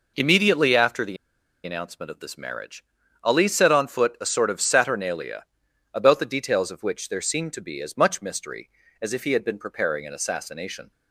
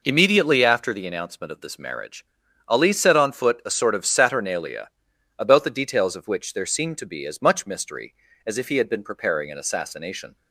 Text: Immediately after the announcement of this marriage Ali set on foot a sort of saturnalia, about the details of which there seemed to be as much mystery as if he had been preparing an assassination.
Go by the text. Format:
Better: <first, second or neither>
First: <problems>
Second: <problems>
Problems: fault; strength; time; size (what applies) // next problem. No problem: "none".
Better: second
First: pauses between "the" and "announcement"; noticeable; at 1.1 s; 0.48 s long // pauses between "marriage" and "Ali"; at 2.8 s; 0.38 s long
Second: pauses between "marriage" and "Ali"; at 2.2 s; 0.41 s long